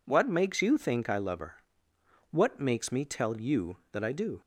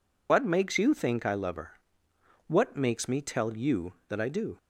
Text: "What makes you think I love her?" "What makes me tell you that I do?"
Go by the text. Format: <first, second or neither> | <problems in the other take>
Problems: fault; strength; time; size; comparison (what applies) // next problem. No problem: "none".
first | loses the start of "What"; at 0.2 s; 65 ms